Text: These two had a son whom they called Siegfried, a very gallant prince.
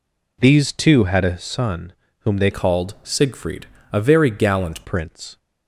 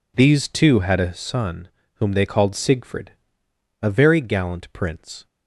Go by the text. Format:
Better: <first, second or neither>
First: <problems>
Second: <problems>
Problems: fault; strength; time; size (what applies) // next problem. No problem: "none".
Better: second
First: pauses between "son" and "whom"; slight; at 1.9 s; 0.28 s long // changes voice from "called" to "gallant"; from 2.5 to 4.8 s; 2.3 s long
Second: pauses between "son" and "whom"; slight; at 1.6 s; 0.27 s long